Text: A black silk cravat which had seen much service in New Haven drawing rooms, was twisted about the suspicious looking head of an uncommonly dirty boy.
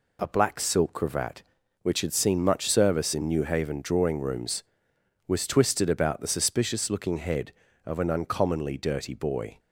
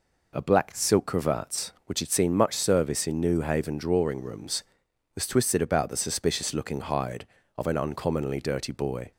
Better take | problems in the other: first | says "hide" for "head"; at 6.7 s

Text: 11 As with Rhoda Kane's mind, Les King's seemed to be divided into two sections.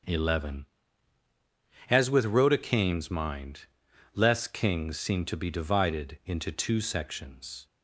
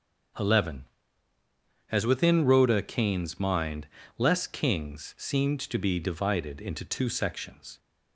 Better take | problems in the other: first | starts louder than the rest; until 2.4 s; 6.5 dB; also in the first // says "within" for "with"; at 2.0 s

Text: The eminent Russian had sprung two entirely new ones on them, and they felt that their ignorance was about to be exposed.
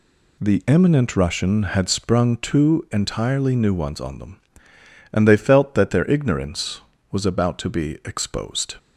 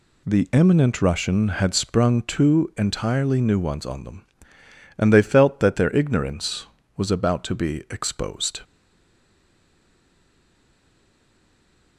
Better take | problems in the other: first | stays silent after the last word; strong; from 8.6 s on; 3.3 s long

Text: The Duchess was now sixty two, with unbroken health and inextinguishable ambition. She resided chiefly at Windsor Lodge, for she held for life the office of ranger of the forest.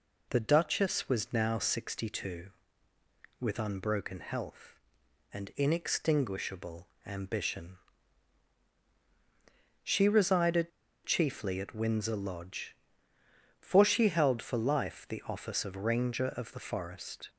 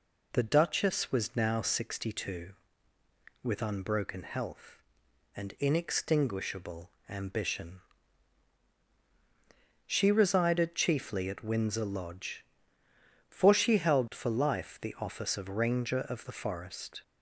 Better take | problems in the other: second | pauses between "inextinguishable" and "ambition"; slight; at 6.8 s; 0.18 s long; slight in the second // pauses between "resided" and "chiefly"; slight; at 10.7 s; 0.35 s long

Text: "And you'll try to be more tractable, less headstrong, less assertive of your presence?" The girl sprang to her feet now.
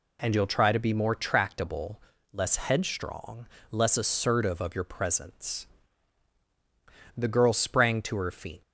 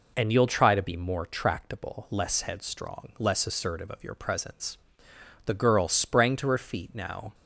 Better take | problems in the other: second | stops before "now"; at 8.6 s

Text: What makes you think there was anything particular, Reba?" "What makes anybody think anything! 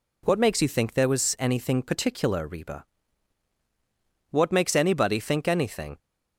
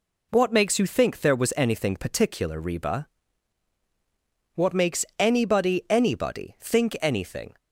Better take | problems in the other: first | pauses between "makes" and "anybody"; slight; at 5.0 s; 0.16 s long // says "anybody" twice; at 5.8 s

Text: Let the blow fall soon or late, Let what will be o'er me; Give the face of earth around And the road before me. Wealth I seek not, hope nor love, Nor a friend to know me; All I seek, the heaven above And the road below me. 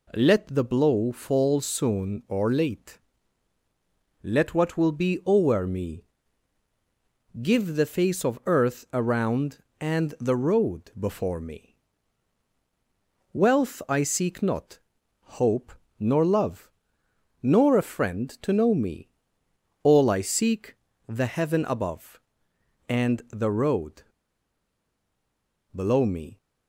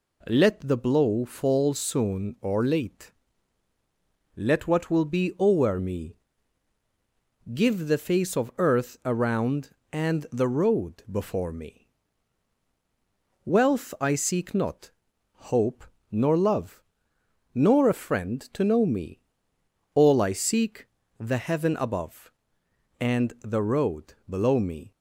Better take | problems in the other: second | pauses between "hope" and "nor"; slight; at 15.7 s; 0.26 s long; slight in the second // pauses between "road" and "below"; strong; at 24.0 s; 1.6 s long

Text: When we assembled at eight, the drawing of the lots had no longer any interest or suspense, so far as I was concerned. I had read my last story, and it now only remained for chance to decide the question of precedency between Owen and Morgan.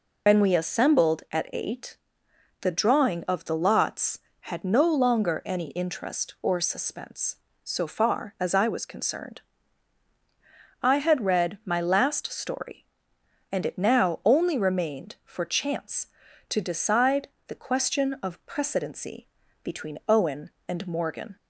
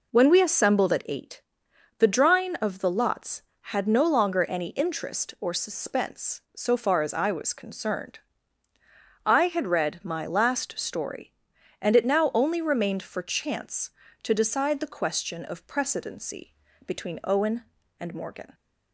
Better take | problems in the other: second | loses the start of "When"; at 0.2 s; 85 ms // pauses between "decide" and "the"; slight; at 17.2 s; 0.20 s long // pauses between "precedency" and "between"; at 19.2 s; 0.38 s long; slight in the second

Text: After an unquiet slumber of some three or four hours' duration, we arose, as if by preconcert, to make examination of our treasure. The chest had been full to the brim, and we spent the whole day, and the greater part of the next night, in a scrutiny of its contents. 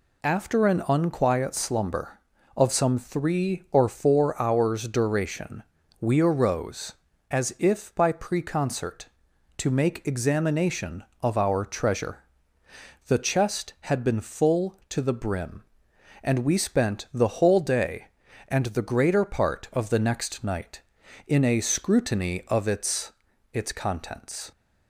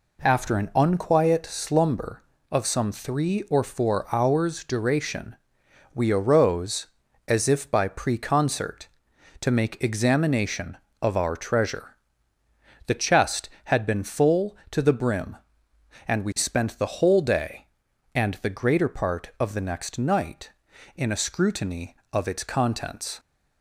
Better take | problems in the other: second | says "its" twice; at 23.5 s

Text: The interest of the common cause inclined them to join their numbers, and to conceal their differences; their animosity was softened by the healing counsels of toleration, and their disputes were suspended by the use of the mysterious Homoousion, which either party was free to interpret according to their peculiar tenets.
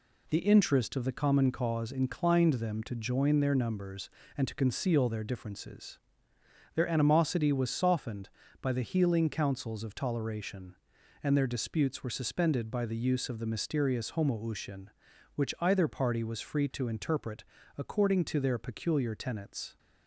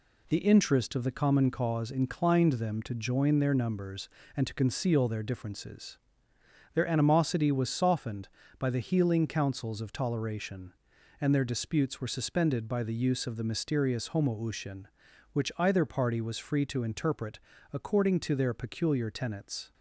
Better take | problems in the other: neither | pauses between "interpret" and "according"; slight; the same in both

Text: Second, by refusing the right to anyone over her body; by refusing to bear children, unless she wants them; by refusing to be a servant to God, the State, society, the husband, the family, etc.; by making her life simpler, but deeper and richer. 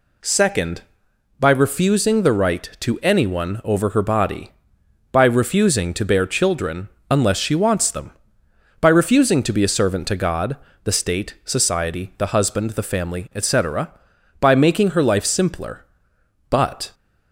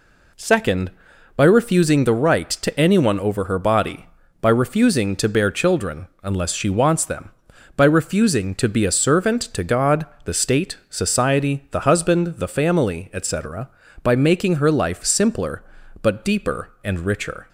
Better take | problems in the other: second | stops before "deeper and richer"; at 16.9 s

